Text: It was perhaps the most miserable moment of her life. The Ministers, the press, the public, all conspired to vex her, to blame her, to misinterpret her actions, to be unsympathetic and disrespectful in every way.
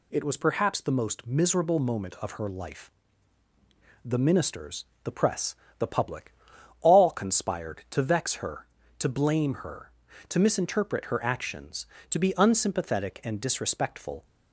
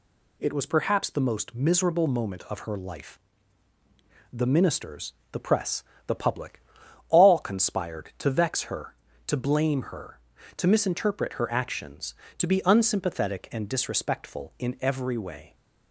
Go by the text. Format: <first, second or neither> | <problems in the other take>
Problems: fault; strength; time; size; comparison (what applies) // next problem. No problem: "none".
second | stops before "in every way"; at 14.2 s